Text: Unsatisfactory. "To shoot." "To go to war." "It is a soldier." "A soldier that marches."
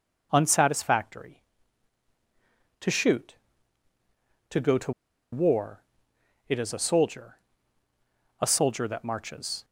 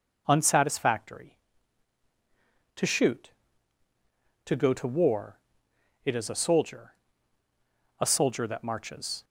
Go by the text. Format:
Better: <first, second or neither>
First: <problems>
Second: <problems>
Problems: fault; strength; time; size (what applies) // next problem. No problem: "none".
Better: second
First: pauses between "to" and "war"; at 4.9 s; 0.40 s long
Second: none